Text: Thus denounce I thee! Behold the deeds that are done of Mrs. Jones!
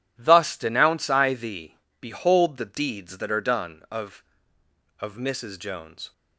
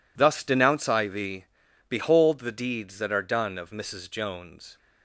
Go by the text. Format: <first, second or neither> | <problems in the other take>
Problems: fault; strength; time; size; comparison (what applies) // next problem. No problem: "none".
second | says "of" twice; at 4.9 s